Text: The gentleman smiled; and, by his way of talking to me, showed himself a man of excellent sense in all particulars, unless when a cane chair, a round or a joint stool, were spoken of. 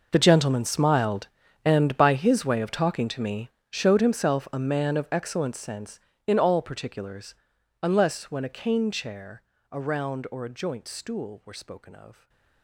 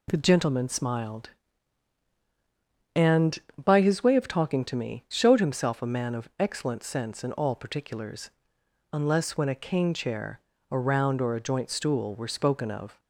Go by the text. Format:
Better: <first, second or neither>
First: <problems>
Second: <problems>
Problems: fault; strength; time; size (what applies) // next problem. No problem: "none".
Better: second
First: gets quieter; strong; throughout; 18 dB // stays silent after the last word; slight; from 12.1 s on; 0.5 s long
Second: none